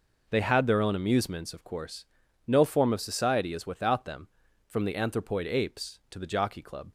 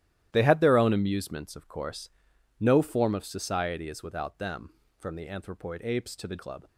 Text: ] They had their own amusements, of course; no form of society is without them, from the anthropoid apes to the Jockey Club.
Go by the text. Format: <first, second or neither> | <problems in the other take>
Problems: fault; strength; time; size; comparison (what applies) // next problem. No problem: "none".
first | starts louder than the rest; strong; until 1.3 s; 13 dB // skips "Jockey"; at 6.3 s